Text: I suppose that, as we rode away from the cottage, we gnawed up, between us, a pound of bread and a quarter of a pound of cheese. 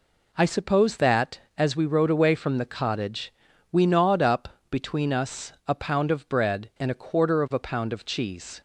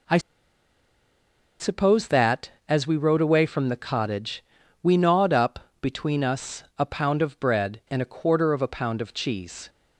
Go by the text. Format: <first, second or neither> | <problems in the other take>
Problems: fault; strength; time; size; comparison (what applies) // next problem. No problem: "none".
first | pauses between "I" and "suppose"; strong; at 0.1 s; 1.4 s long